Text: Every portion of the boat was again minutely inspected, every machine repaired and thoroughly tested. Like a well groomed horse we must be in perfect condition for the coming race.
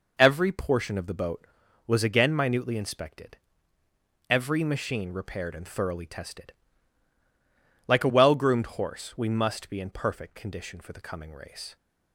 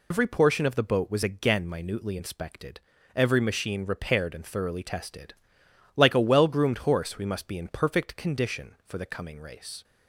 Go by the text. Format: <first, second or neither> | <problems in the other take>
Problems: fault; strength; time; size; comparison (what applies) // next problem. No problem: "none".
first | loses the start of "Every"; at 0.1 s; 85 ms